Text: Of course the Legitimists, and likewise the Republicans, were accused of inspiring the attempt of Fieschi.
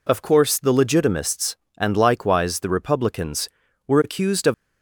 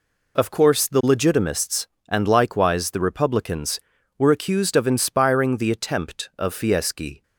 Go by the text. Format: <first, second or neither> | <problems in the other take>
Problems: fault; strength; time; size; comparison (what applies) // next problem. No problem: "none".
second | stops before "inspiring the attempt of Fieschi"; at 4.5 s